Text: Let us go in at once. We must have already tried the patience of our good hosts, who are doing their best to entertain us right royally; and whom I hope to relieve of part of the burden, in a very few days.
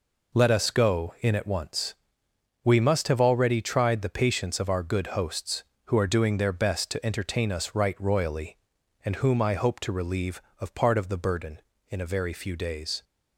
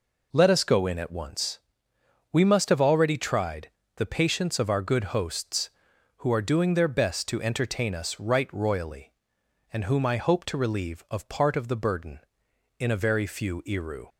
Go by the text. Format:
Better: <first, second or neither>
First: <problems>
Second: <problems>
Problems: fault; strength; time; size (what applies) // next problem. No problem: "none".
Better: first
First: none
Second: pauses between "tried" and "the"; slight; at 3.7 s; 0.26 s long // says "iru" for "days"; at 13.6 s